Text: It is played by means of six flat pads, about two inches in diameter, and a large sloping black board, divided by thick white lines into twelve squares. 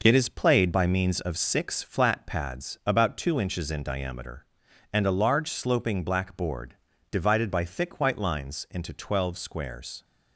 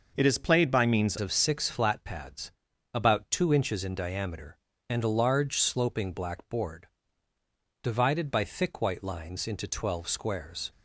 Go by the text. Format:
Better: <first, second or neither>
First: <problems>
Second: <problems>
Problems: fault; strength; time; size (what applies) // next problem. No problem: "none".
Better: first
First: none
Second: changes voice at "of"; from 1.2 s on; 9.5 s long